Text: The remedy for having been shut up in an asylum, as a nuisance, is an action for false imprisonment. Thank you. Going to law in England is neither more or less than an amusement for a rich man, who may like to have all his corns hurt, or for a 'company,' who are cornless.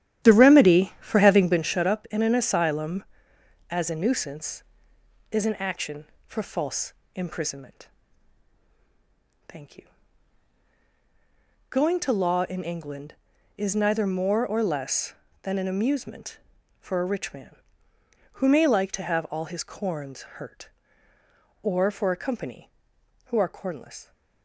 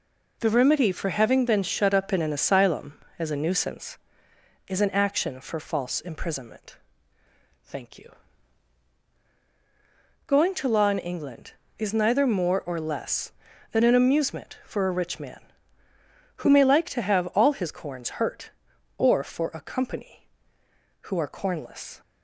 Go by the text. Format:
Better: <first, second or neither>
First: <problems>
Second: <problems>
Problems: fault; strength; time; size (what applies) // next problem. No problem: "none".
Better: second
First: starts louder than the rest; strong; until 1.6 s; 11.5 dB // pauses between "false" and "imprisonment"; slight; at 6.9 s; 0.24 s long // pauses between "corns" and "hurt"; slight; at 20.2 s; 0.16 s long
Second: none